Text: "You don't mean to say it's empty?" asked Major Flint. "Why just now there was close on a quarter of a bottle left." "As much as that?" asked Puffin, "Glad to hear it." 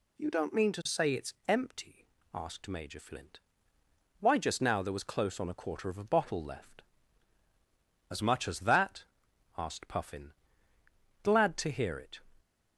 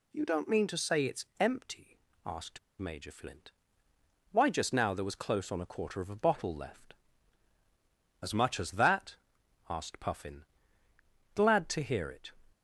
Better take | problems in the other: first | pauses between "asked" and "Major"; slight; at 2.5 s; 0.20 s long

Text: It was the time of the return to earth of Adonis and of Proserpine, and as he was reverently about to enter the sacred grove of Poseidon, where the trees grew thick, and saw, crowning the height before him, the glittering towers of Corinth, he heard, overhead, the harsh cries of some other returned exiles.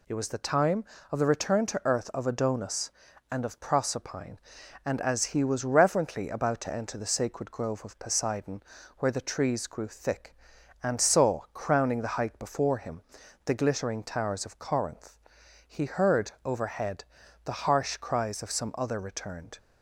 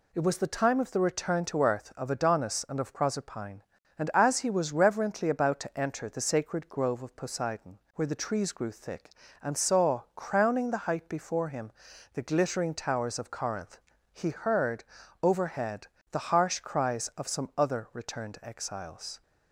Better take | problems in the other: second | stops before "exiles"; at 19.5 s

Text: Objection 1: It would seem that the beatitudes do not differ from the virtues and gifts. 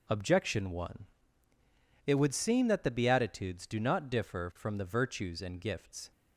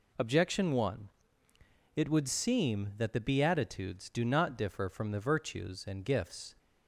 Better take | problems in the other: neither | none

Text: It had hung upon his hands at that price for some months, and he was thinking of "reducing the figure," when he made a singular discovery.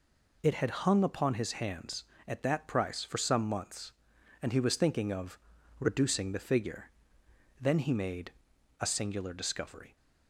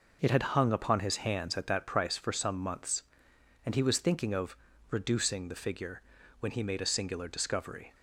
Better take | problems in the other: second | pauses between "of" and "reducing"; at 5.3 s; 0.42 s long; slight in the second // says "then" for "when"; at 7.5 s // pauses between "made" and "a"; noticeable; at 8.3 s; 0.48 s long

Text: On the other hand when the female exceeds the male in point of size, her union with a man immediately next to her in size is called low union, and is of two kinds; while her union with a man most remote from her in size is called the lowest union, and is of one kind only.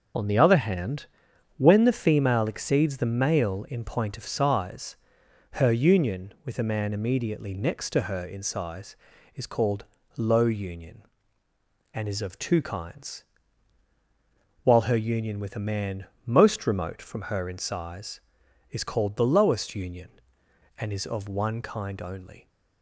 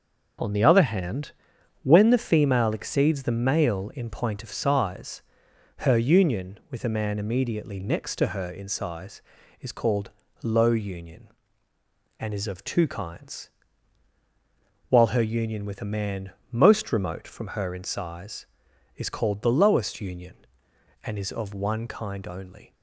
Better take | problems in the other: second | loses the start of "On"; at 0.1 s; 20 ms // pauses between "hand" and "when"; noticeable; at 1.0 s; 0.50 s long; noticeable in the second // pauses between "called" and "low"; slight; at 9.8 s; 0.32 s long; slight in the second // pauses between "man" and "most"; slight; at 16.0 s; 0.20 s long; slight in the second

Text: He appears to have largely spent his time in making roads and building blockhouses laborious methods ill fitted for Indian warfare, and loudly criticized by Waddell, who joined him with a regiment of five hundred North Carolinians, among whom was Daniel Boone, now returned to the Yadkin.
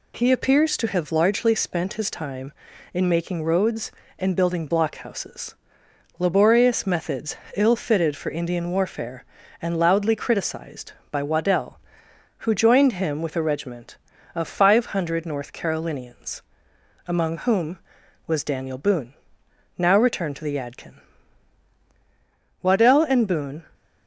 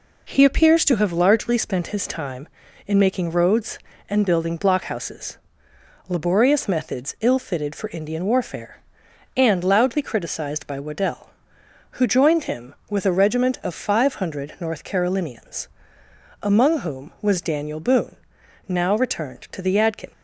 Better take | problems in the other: second | pauses between "blockhouses" and "laborious"; noticeable; at 5.5 s; 0.64 s long; noticeable in the second // pauses between "methods" and "ill"; slight; at 7.3 s; 0.22 s long // goes on to say "Waddell and Boone"; noticeable; from 22.6 s on; 1.0 s long

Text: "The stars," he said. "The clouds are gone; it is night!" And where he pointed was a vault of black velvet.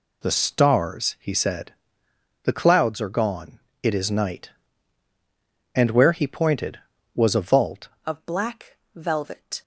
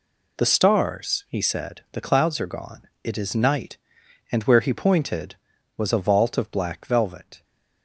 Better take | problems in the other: second | changes voice at "of"; from 8.0 s on; 1.6 s long // pauses between "black" and "velvet"; slight; at 8.7 s; 0.18 s long

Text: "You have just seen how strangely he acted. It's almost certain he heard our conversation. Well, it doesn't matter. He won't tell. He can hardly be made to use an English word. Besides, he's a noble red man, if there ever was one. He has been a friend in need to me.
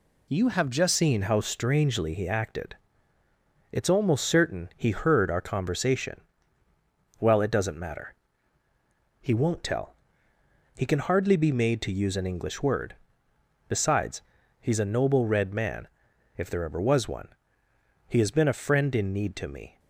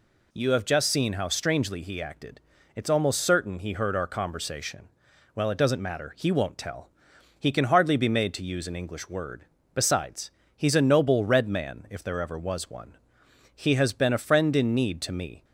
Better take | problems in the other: second | changes voice at "seen"; from 0.9 s on; 18.8 s long

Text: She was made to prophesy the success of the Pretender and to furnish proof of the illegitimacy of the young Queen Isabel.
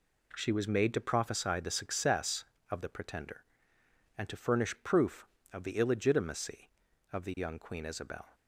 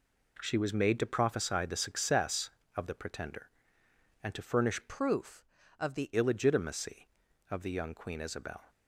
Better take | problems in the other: first | changes voice from "proof" to "the"; from 4.8 to 6.1 s; 1.3 s long

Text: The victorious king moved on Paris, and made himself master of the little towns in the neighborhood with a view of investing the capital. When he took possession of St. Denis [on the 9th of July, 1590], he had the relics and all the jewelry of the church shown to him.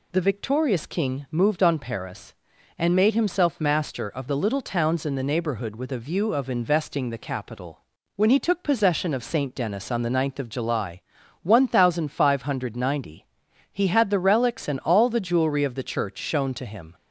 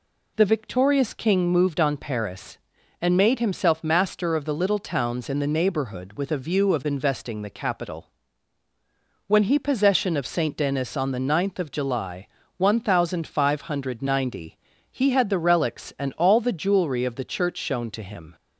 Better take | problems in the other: first | skips "took"; at 9.5 s

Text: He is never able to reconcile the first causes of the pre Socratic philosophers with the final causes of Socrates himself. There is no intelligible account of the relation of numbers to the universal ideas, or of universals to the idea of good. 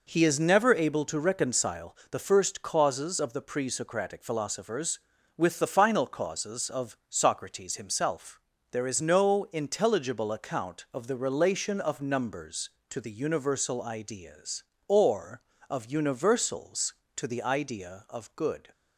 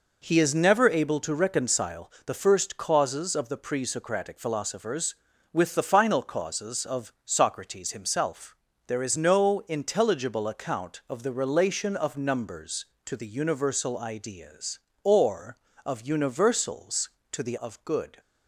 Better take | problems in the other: first | pauses between "reconcile" and "the"; slight; at 2.0 s; 0.18 s long; slight in the first // skips "idea"; at 17.5 s

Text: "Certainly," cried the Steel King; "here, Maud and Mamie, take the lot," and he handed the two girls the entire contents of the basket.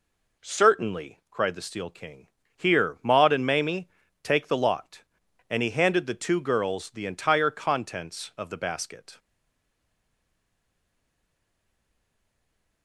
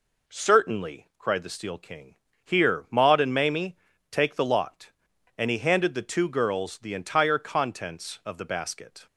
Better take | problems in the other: second | stays silent after the last word; strong; from 9.1 s on; 3.7 s long

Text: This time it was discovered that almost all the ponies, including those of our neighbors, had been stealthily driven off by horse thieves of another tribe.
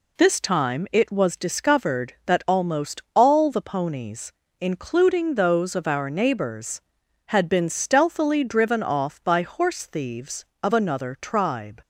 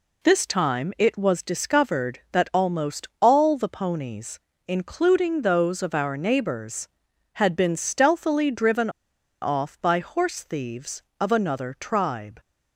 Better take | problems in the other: first | pauses between "driven" and "off"; noticeable; at 8.8 s; 0.52 s long

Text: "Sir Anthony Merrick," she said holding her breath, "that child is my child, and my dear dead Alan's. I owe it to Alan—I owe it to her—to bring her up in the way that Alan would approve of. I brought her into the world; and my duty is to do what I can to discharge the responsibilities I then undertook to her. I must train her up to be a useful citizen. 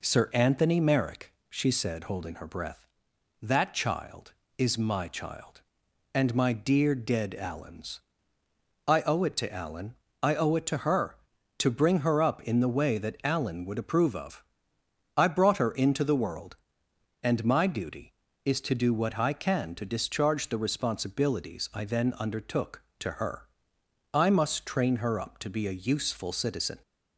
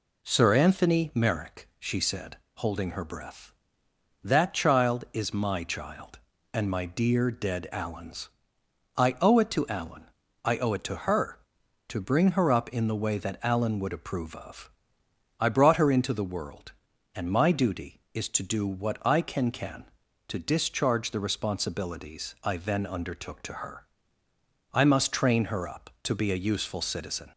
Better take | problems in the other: first | pauses between "said" and "holding"; slight; at 2.3 s; 0.20 s long // says "can" twice; at 19.4 s

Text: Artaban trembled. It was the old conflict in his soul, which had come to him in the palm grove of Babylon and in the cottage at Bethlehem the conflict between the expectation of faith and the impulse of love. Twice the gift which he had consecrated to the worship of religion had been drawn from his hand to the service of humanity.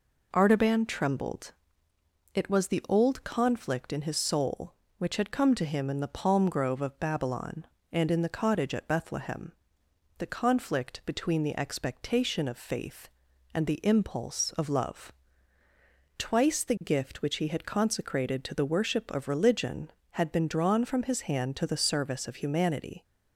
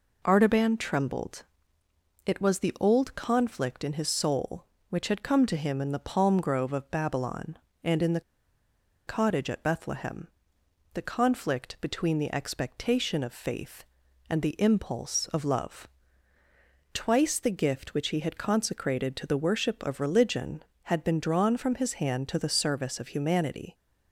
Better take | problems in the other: first | pauses between "the" and "cottage"; noticeable; at 8.1 s; 0.87 s long // pauses between "Bethlehem" and "the"; noticeable; at 10.2 s; 0.66 s long; noticeable in the first

